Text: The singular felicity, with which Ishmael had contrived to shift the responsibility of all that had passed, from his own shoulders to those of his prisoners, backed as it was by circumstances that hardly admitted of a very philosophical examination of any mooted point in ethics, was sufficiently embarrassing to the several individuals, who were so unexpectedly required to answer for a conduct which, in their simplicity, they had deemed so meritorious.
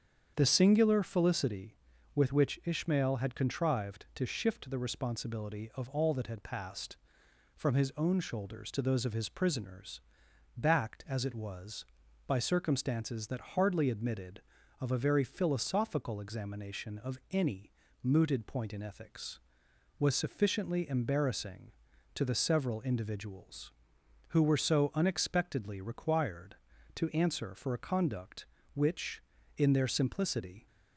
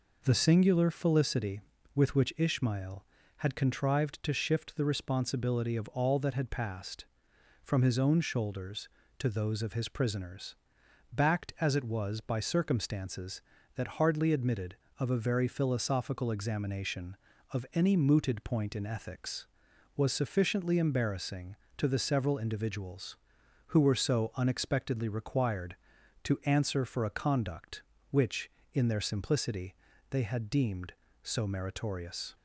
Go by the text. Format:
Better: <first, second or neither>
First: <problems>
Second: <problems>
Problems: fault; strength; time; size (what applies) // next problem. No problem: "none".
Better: second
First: starts louder than the rest; strong; until 1.3 s; 7.5 dB // pauses between "any" and "mooted"; slight; at 17.7 s; 0.32 s long // stops before "they had deemed so meritorious"; at 30.6 s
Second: none